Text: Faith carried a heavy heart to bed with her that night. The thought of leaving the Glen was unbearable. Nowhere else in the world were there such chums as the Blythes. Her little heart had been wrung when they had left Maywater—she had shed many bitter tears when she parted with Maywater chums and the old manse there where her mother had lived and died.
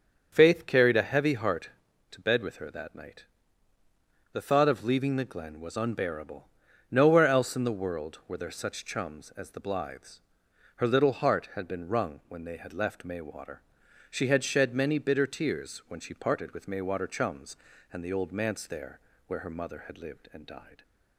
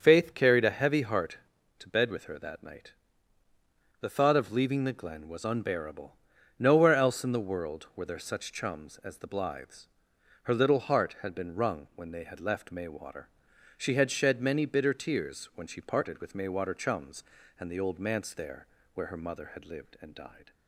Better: neither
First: starts louder than the rest; until 1.3 s; 7 dB // pauses between "there" and "where"; slight; at 18.9 s; 0.28 s long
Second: starts louder than the rest; until 1.0 s; 6.5 dB // pauses between "there" and "where"; slight; at 18.6 s; 0.28 s long

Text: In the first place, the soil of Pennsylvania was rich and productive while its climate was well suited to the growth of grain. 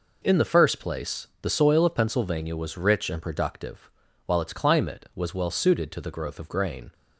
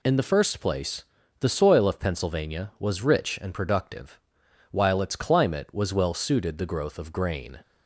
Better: first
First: pauses between "productive" and "while"; slight; at 3.8 s; 0.36 s long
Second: pauses between "productive" and "while"; noticeable; at 4.1 s; 0.54 s long // skips "to"; at 6.5 s

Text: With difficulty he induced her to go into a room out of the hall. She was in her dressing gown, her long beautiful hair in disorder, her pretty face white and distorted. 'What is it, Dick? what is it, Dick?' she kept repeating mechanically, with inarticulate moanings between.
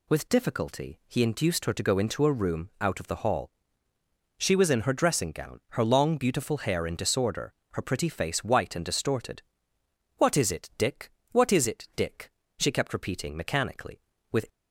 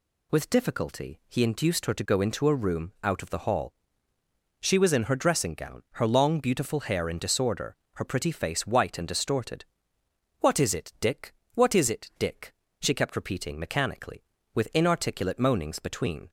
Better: second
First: stops before "inarticulate moanings between"; at 14.4 s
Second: none

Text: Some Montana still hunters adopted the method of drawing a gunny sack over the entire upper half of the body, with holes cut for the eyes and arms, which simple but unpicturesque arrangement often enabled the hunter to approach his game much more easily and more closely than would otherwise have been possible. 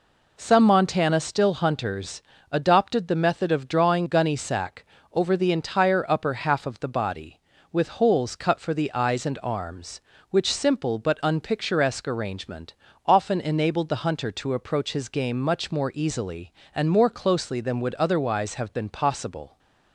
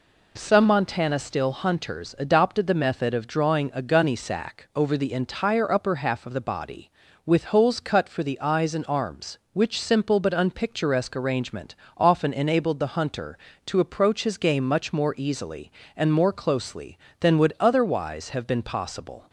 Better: second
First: pauses between "hunters" and "adopted"; slight; at 2.2 s; 0.30 s long // skips "a"; at 4.0 s // pauses between "sack" and "over"; slight; at 4.8 s; 0.28 s long // pauses between "arrangement" and "often"; slight; at 12.7 s; 0.30 s long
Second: pauses between "arrangement" and "often"; slight; at 11.7 s; 0.20 s long

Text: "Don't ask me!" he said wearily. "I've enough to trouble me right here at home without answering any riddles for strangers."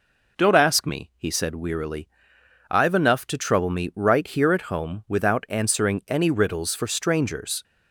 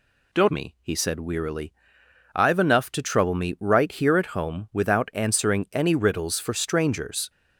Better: first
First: none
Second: skips "ask"; at 0.4 s

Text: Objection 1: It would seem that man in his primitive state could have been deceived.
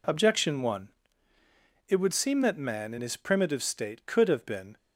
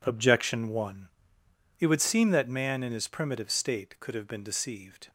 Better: second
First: stops before "deceived"; at 4.7 s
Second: none

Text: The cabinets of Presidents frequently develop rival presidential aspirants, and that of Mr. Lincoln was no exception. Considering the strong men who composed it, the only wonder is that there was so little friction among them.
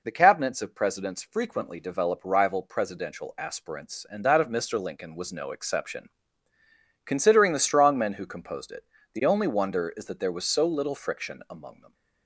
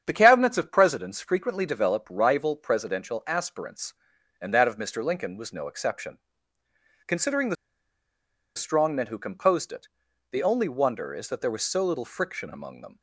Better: first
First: none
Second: starts louder than the rest; strong; until 1.0 s; 8.5 dB // pauses between "the" and "strong"; at 7.5 s; 1.0 s long

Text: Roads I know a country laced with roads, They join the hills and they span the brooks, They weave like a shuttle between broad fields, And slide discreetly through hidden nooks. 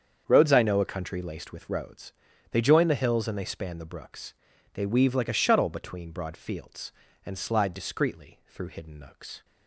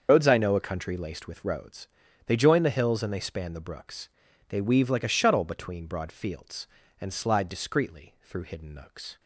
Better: first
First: starts louder than the rest; strong; until 1.2 s; 7.5 dB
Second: loses the start of "Roads"; at 0.0 s; 75 ms // starts louder than the rest; until 1.1 s; 6.5 dB

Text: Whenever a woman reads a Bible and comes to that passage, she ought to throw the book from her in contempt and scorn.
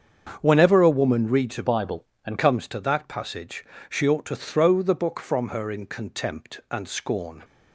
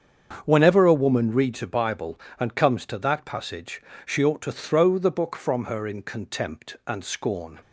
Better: second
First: starts louder than the rest; strong; until 1.4 s; 7.5 dB // changes voice from "Bible" to "and"; from 1.6 to 2.3 s; 0.7 s long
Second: starts louder than the rest; strong; until 1.4 s; 7.5 dB

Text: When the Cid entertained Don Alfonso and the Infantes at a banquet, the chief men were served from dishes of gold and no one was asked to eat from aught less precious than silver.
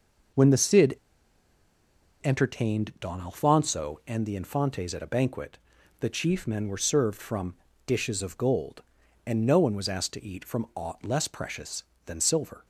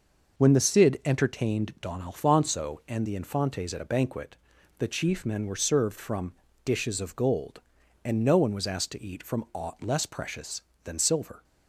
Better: second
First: pauses between "Cid" and "entertained"; strong; at 0.9 s; 1.2 s long // pauses between "from" and "dishes"; slight; at 7.5 s; 0.30 s long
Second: pauses between "from" and "dishes"; slight; at 6.3 s; 0.30 s long

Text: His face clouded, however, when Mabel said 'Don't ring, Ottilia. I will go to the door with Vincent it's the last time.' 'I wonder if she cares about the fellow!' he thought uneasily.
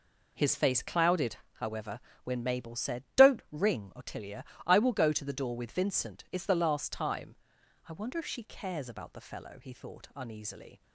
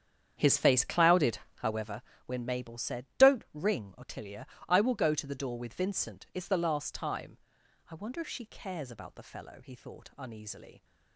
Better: first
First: none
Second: starts louder than the rest; strong; until 2.0 s; 8.5 dB

